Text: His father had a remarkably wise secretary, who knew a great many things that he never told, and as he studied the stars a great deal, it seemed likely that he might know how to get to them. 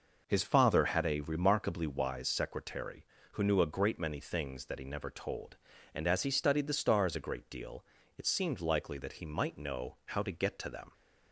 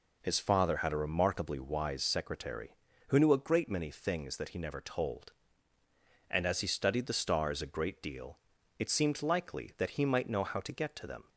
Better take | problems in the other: neither | none

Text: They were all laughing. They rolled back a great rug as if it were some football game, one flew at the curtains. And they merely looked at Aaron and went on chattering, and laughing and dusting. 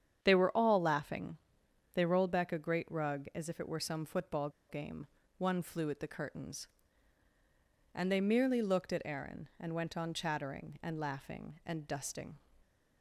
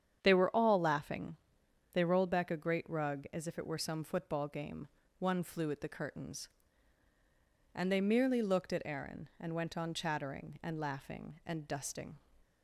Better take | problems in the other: second | starts louder than the rest; strong; until 1.2 s; 8.5 dB; strong in the second // pauses between "football" and "game"; slight; at 4.4 s; 0.20 s long

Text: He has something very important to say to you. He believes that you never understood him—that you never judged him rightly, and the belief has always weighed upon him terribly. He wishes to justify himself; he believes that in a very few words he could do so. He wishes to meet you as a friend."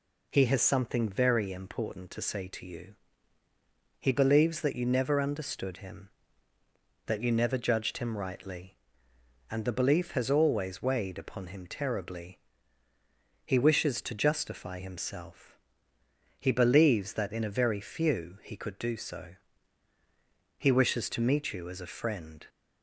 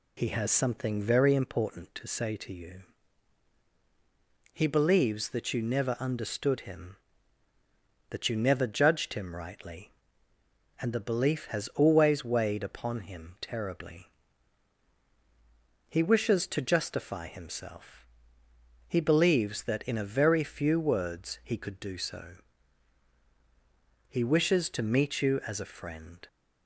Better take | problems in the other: second | skips "words"; at 18.4 s

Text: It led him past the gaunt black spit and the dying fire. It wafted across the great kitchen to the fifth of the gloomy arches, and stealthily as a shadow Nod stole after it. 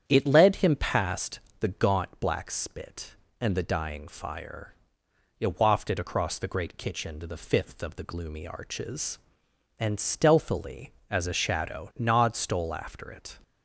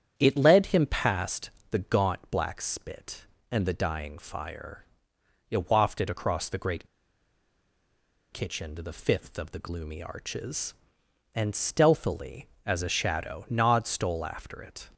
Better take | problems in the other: first | starts louder than the rest; strong; until 1.1 s; 9 dB; strong in the first // pauses between "past" and "the"; slight; at 1.5 s; 0.20 s long; slight in the first // pauses between "great" and "kitchen"; strong; at 6.8 s; 1.4 s long

